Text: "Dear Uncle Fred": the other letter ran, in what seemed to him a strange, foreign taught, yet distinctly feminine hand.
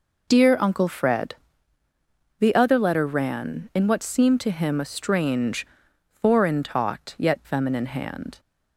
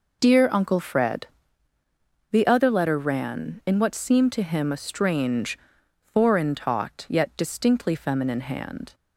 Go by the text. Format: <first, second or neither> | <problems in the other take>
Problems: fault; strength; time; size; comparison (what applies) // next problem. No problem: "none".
second | skips "distinctly"; at 7.4 s